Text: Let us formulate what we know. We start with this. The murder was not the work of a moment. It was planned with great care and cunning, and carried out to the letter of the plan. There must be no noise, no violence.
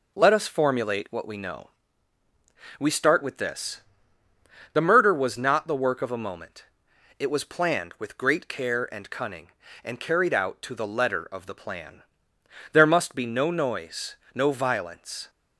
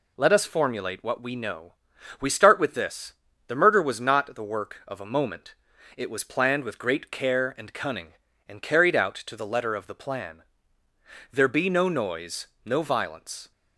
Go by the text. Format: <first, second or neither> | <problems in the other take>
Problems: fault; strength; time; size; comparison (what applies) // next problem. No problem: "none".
first | skips "must"; at 11.4 s